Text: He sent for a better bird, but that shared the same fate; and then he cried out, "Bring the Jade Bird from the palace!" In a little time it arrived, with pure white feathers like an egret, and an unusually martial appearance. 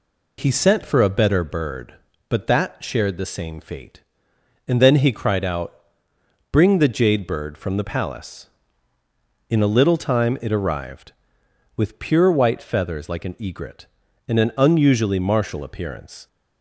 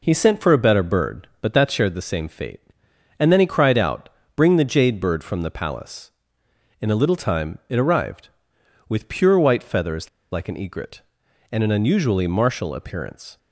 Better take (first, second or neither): first